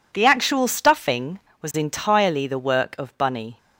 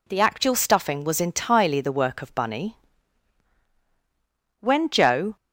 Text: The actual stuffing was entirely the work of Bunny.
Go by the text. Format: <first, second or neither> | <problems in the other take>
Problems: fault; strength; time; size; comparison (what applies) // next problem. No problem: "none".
first | goes on to say "When Joe"; noticeable; from 4.5 s on; 0.76 s long